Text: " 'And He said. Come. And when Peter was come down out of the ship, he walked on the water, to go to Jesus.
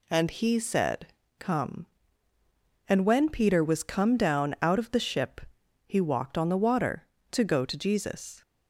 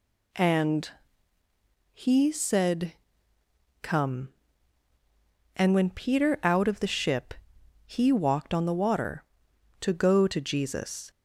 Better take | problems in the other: first | pauses between "And" and "He"; at 0.8 s; 1.0 s long // skips "was come down"; at 6.4 s

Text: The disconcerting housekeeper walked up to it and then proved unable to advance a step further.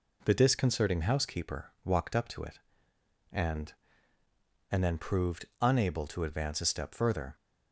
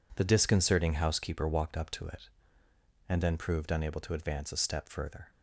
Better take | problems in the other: second | says "and" twice; at 4.6 s // pauses between "proved" and "unable"; slight; at 5.4 s; 0.16 s long

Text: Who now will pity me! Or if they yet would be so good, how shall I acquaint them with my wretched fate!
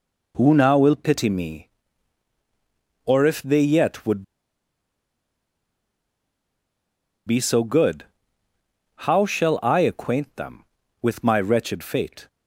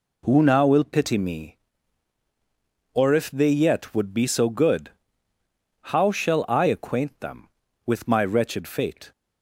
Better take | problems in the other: second | pauses between "would" and "be"; strong; at 4.2 s; 3.0 s long

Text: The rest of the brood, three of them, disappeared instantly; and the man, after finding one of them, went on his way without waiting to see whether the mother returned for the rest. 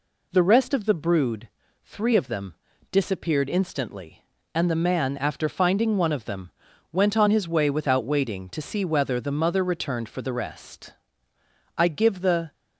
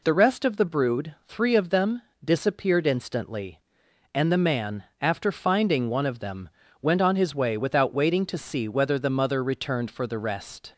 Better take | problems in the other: second | goes on to say "I give the"; noticeable; from 11.7 s on; 0.74 s long

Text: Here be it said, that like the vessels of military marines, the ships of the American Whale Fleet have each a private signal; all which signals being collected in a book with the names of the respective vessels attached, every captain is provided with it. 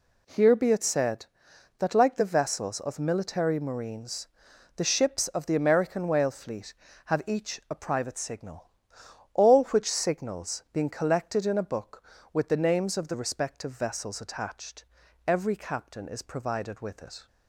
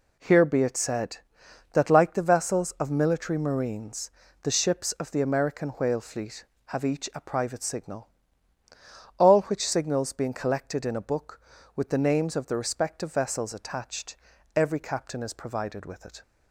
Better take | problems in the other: neither | none

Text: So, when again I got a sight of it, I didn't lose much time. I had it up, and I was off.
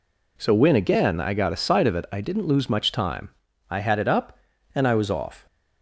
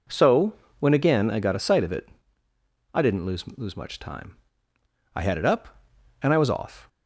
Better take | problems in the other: first | says "lose" twice; at 3.5 s

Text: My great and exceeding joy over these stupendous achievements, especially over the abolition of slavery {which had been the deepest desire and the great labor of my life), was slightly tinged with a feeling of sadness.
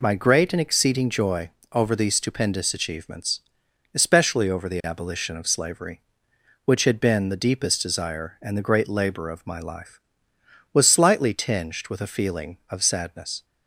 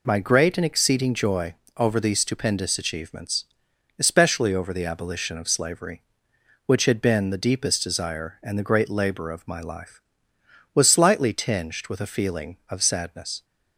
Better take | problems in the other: neither | pauses between "joy" and "over"; slight; the same in both

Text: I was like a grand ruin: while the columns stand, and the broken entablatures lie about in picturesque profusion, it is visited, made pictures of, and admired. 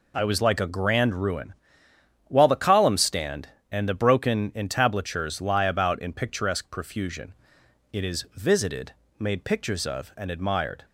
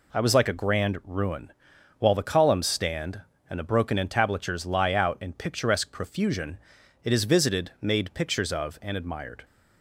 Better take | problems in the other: first | says "out" for "about"; at 4.9 s

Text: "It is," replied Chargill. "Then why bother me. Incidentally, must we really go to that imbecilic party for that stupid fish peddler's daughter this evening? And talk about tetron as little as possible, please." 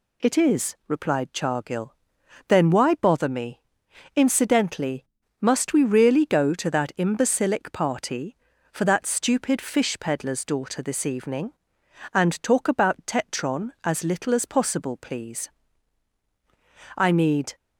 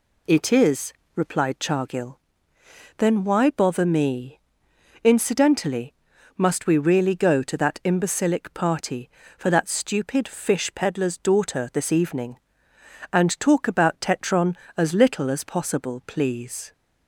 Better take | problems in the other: second | goes on to say "I need"; from 16.9 s on; 0.58 s long

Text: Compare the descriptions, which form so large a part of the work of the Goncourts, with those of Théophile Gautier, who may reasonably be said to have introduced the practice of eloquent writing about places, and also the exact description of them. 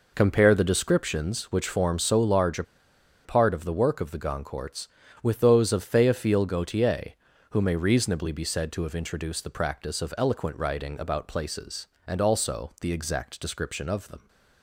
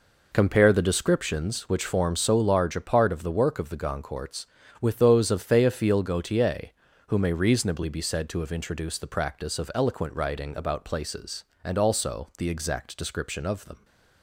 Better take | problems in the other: second | pauses between "a" and "part"; noticeable; at 2.6 s; 0.61 s long

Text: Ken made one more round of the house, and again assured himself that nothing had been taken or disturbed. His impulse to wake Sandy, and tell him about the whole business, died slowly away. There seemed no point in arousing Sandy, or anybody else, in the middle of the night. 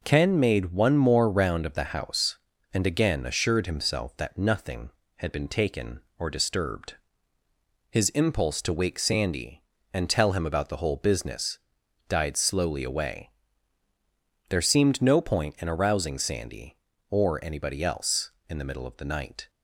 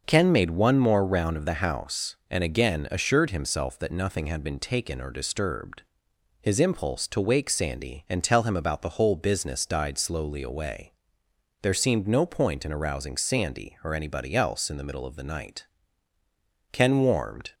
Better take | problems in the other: first | starts louder than the rest; until 1.0 s; 6.5 dB // goes on to say "Ken warmed"; noticeable; from 16.7 s on; 0.82 s long

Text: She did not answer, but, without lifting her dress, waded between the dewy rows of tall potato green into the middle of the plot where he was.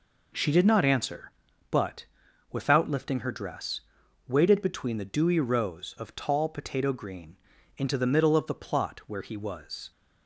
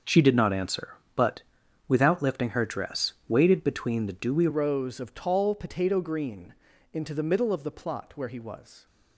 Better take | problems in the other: first | starts louder than the rest; until 1.2 s; 6.5 dB // changes voice at "rows"; from 4.5 s on; 4.3 s long // pauses between "green" and "into"; at 6.5 s; 0.40 s long; also in the first

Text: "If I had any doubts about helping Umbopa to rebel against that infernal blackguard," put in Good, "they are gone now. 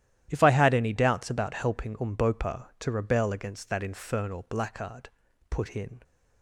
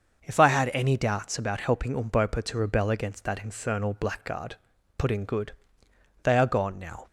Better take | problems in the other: second | starts louder than the rest; strong; until 1.3 s; 12.5 dB; also in the second // stops before "Good they are gone now"; at 6.0 s

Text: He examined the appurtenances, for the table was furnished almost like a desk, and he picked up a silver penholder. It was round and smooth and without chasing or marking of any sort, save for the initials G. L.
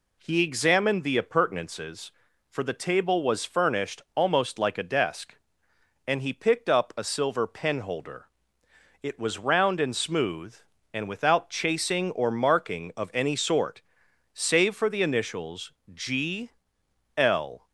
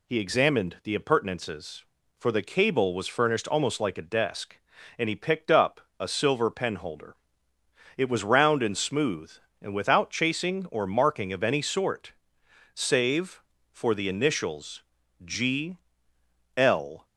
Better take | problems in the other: first | says "cable" for "table"; at 2.4 s // pauses between "up" and "a"; slight; at 5.8 s; 0.18 s long // pauses between "initials" and "G"; at 14.8 s; 0.40 s long; slight in the first // pauses between "G" and "L"; noticeable; at 15.7 s; 0.78 s long; noticeable in the first

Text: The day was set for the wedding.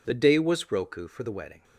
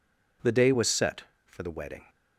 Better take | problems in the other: second | says "roku" for "set"; at 0.6 s

